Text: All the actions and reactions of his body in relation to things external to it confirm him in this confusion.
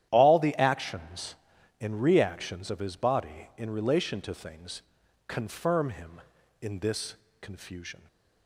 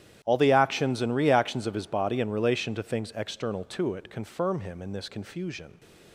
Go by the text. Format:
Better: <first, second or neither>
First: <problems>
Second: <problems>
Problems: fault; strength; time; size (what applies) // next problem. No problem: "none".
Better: second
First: starts louder than the rest; strong; until 1.1 s; 11.5 dB // skips "external to it"; at 5.0 s // pauses between "this" and "confusion"; slight; at 7.1 s; 0.26 s long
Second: starts louder than the rest; strong; until 1.2 s; 11.5 dB